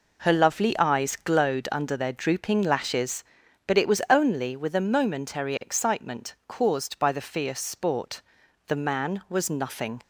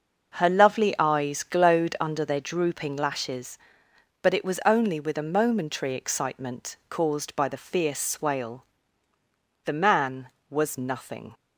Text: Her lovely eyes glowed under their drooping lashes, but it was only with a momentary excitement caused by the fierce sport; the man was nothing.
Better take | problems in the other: first | starts louder than the rest; noticeable; until 1.3 s; 6 dB // says "swale" for "sport"; at 7.9 s

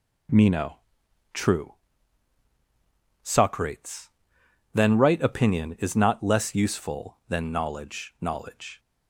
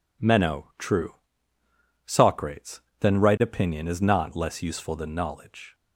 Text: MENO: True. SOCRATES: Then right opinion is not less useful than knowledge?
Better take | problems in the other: second | says "knowledge" twice; at 8.2 s

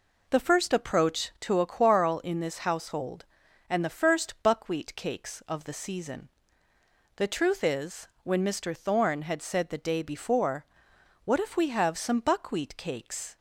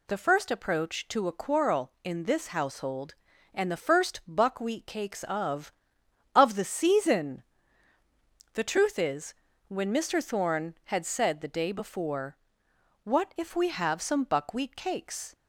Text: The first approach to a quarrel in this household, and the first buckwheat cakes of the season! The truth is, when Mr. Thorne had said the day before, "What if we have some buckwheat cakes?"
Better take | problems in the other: first | says "of" twice; at 6.3 s

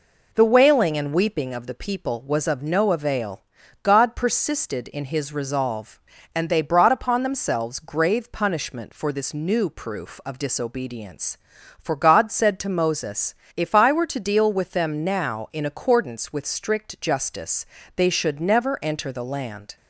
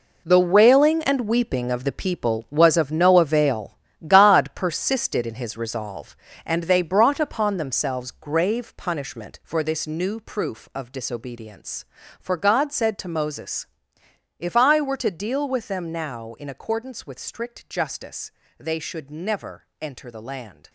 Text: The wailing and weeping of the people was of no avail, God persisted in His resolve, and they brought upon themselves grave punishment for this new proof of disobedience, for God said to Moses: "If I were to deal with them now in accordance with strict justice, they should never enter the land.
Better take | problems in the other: first | gets quieter; strong; throughout; 12 dB // pauses between "never" and "enter"; slight; at 19.6 s; 0.16 s long

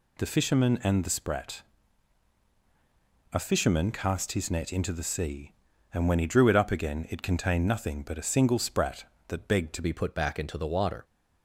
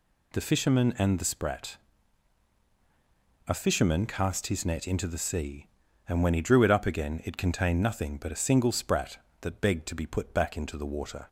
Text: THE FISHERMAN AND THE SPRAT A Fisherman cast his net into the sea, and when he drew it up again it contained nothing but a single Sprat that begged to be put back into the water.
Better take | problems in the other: second | pauses between "SPRAT" and "A"; strong; at 1.6 s; 1.7 s long; strong in the second // changes voice at "be"; from 9.8 s on; 1.2 s long

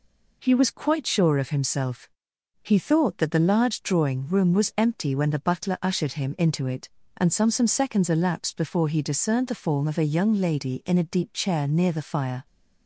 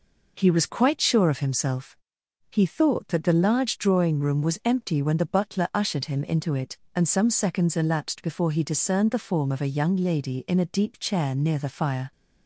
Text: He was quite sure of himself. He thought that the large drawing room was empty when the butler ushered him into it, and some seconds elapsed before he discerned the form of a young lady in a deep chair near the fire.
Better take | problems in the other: second | says "some" twice; at 7.5 s

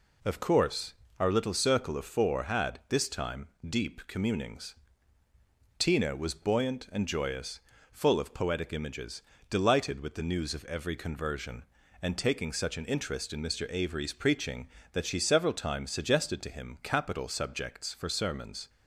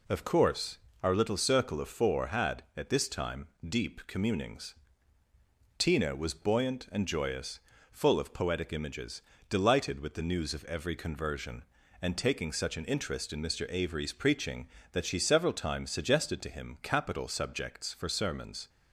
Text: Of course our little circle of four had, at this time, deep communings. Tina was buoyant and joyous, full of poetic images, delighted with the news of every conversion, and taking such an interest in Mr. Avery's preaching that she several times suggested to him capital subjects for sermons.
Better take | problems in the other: second | pauses between "course" and "our"; slight; at 0.9 s; 0.26 s long; slight in the second // skips "at"; at 2.8 s

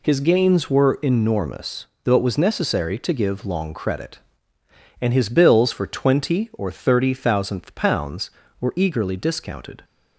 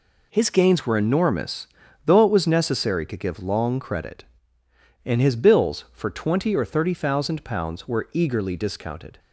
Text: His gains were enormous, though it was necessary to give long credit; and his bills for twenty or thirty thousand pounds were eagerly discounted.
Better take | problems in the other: second | says "thousandth" for "thousand"; at 7.1 s

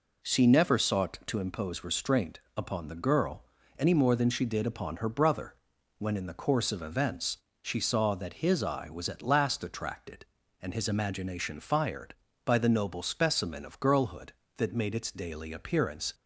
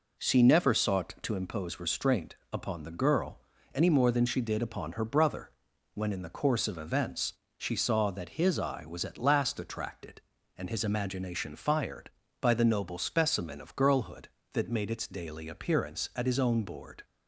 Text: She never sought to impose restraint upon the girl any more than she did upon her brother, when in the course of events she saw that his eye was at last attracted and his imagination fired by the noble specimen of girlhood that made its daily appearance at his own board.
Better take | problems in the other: second | pauses between "restraint" and "upon"; slight; at 2.3 s; 0.18 s long; slight in the second // pauses between "girl" and "any"; slight; at 3.4 s; 0.34 s long; slight in the second // pauses between "events" and "she"; slight; at 7.3 s; 0.24 s long; slight in the second // stops before "at his own board"; at 16.1 s

